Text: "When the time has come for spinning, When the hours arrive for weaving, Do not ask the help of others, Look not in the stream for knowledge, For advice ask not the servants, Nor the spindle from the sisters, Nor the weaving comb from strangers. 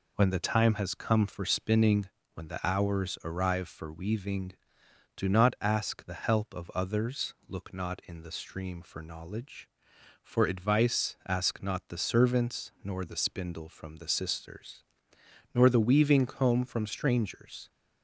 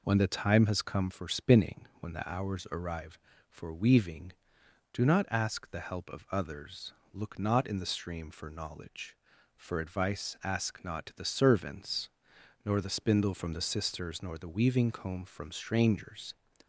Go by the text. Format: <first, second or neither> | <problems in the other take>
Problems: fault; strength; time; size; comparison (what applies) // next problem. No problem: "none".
neither | none